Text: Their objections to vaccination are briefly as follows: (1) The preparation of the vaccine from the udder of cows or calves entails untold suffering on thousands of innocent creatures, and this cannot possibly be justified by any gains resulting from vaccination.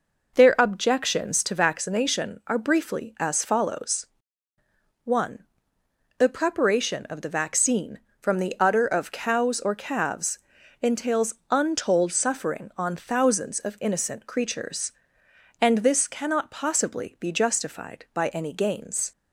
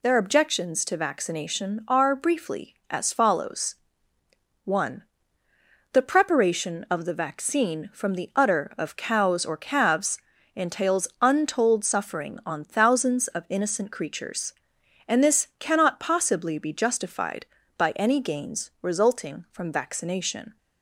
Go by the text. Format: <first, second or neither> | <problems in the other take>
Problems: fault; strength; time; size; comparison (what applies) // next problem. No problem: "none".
second | pauses between "calves" and "entails"; at 10.3 s; 0.44 s long; slight in the second // pauses between "entails" and "untold"; slight; at 11.3 s; 0.16 s long // stops before "resulting from vaccination"; at 19.1 s